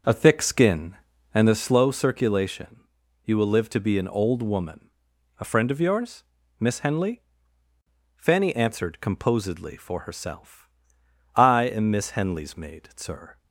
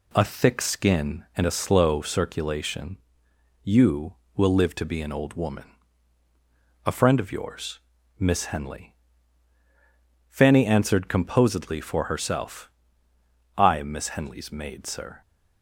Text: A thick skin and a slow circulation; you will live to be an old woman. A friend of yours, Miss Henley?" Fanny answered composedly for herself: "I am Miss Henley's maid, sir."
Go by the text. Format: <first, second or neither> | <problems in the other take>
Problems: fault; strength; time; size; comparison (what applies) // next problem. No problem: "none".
second | starts louder than the rest; noticeable; until 1.6 s; 6 dB